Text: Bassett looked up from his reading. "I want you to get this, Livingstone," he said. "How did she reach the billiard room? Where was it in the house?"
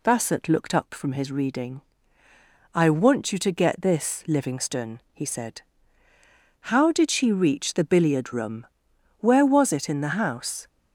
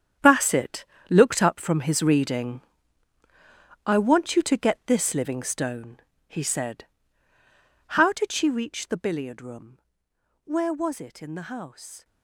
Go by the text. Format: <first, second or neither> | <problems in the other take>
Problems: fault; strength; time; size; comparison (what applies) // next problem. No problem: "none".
first | gets quieter; strong; throughout; 13 dB // pauses between "Bassett" and "looked"; slight; at 0.8 s; 0.24 s long